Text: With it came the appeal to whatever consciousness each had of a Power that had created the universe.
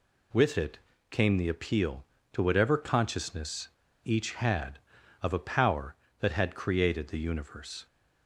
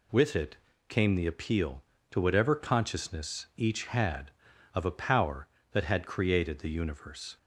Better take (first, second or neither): second